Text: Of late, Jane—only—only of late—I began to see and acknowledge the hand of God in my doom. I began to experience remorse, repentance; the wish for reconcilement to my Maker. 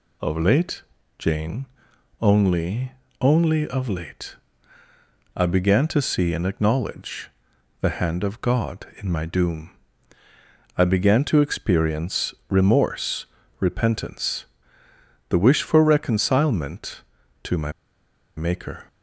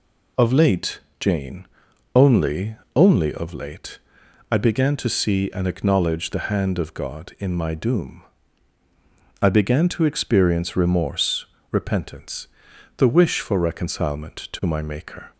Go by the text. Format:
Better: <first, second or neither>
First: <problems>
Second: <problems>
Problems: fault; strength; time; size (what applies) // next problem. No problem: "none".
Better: second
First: pauses between "acknowledge" and "the"; noticeable; at 7.2 s; 0.50 s long // pauses between "experience" and "remorse"; slight; at 12.3 s; 0.16 s long // pauses between "my" and "Maker"; noticeable; at 17.7 s; 0.65 s long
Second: none